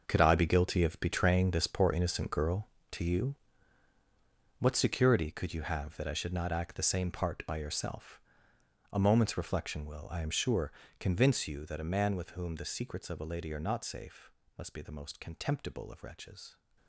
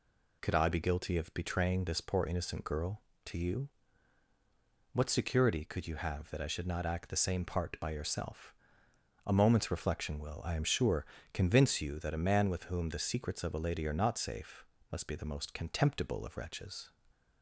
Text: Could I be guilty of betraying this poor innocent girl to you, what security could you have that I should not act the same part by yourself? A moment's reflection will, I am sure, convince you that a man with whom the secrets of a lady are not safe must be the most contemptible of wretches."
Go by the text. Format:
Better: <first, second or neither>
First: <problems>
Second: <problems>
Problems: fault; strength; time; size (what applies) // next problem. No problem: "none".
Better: second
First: gets quieter; strong; throughout; 12.5 dB // pauses between "safe" and "must"; slight; at 14.3 s; 0.24 s long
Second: pauses between "safe" and "must"; slight; at 14.6 s; 0.24 s long